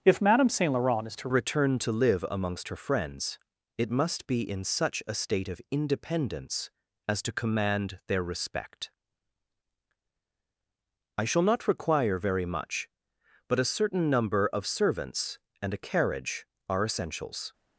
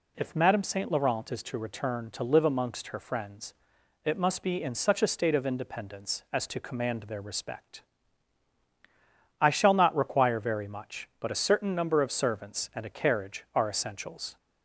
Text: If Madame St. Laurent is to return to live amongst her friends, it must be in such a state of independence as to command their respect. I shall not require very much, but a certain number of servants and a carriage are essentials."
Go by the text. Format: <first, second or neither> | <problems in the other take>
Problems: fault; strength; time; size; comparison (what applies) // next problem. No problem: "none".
second | starts louder than the rest; strong; until 1.0 s; 7.5 dB // changes voice at "return"; from 1.3 s on; 16.2 s long